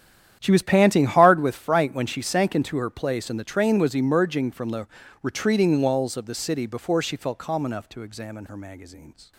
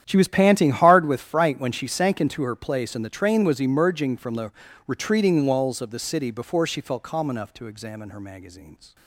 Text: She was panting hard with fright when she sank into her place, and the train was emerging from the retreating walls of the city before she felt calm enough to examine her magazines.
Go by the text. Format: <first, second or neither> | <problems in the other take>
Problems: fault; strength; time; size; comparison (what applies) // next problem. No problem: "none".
neither | starts louder than the rest; strong; the same in both // pauses between "the" and "retreating"; slight; the same in both